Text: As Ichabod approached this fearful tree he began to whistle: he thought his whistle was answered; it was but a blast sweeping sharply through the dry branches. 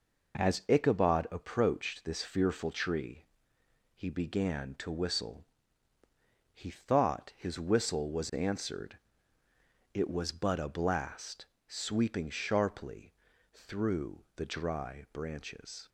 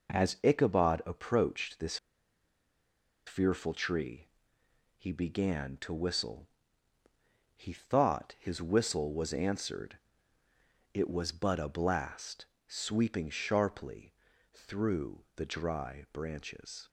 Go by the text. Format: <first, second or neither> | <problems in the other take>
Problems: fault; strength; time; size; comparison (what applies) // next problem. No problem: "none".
first | pauses between "this" and "fearful"; strong; at 1.9 s; 1.2 s long // pauses between "tree" and "he"; noticeable; at 4.2 s; 0.72 s long; noticeable in the first // pauses between "blast" and "sweeping"; slight; at 12.4 s; 0.20 s long; slight in the first // pauses between "sharply" and "through"; at 14.1 s; 0.38 s long; also in the first